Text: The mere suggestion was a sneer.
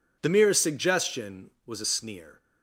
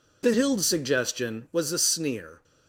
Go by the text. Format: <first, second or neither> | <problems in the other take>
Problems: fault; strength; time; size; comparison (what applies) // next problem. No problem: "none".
first | says "hild" for "mere"; at 0.3 s